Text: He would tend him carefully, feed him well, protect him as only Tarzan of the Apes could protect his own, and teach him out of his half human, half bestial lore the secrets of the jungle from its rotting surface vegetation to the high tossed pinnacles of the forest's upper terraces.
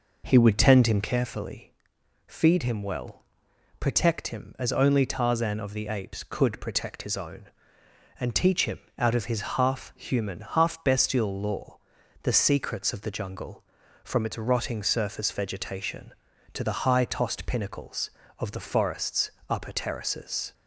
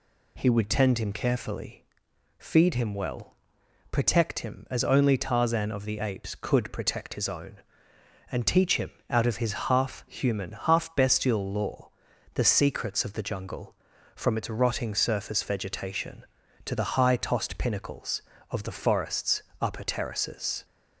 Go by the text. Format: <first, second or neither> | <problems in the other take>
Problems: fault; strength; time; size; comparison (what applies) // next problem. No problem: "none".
second | starts louder than the rest; noticeable; until 1.1 s; 5 dB // pauses between "him" and "out"; slight; at 8.7 s; 0.18 s long; slight in the second // pauses between "lore" and "the"; noticeable; at 11.7 s; 0.46 s long; noticeable in the second // pauses between "forest's" and "upper"; slight; at 19.2 s; 0.18 s long; slight in the second